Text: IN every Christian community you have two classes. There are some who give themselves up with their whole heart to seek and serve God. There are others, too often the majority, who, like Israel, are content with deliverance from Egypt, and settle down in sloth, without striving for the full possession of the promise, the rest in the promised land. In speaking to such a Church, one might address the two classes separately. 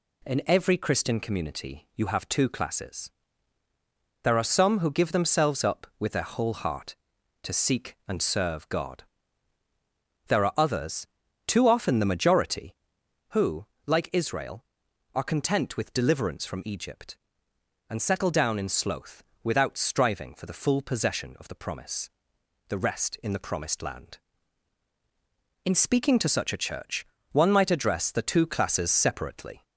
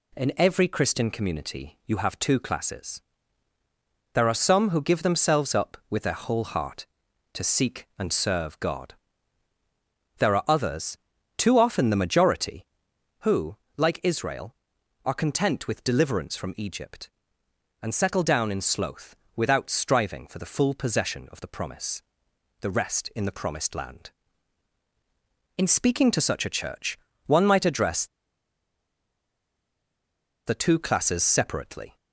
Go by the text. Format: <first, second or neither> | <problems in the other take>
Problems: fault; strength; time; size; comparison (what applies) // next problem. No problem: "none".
first | pauses between "address" and "the"; strong; at 28.0 s; 2.4 s long